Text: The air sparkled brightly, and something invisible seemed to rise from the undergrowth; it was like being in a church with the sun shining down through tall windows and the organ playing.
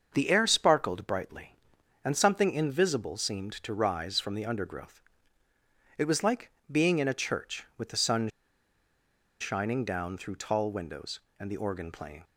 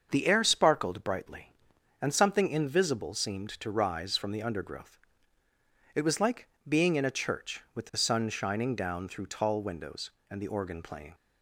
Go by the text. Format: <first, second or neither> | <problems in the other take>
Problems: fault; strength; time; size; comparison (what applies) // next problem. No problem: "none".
second | starts louder than the rest; until 1.1 s; 6.5 dB; also in the second // pauses between "like" and "being"; slight; at 6.4 s; 0.20 s long; slight in the second // pauses between "sun" and "shining"; at 8.2 s; 1.1 s long